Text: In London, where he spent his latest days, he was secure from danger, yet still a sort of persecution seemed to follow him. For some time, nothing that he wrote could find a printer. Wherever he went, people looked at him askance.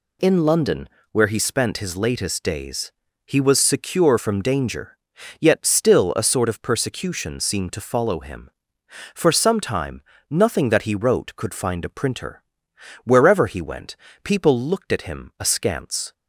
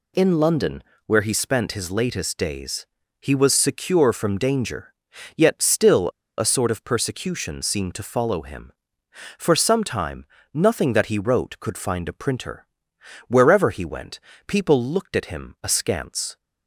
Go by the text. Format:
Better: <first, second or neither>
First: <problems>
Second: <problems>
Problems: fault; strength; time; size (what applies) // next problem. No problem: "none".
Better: first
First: none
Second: pauses between "still" and "a"; slight; at 6.0 s; 0.29 s long